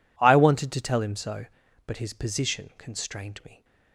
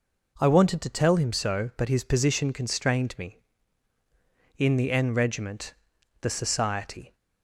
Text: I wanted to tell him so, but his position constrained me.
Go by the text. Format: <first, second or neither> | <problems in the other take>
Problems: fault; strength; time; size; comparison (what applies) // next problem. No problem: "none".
first | goes on to say "In the N regiment the society"; strong; from 4.5 s on; 2.5 s long